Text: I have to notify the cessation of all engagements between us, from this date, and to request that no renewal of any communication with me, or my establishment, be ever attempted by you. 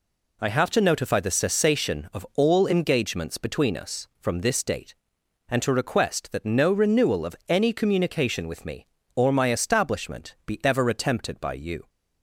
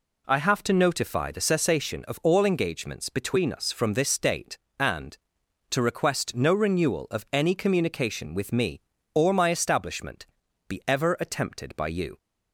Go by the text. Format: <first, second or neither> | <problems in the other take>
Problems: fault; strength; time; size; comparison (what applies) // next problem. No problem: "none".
first | skips "that"; at 6.3 s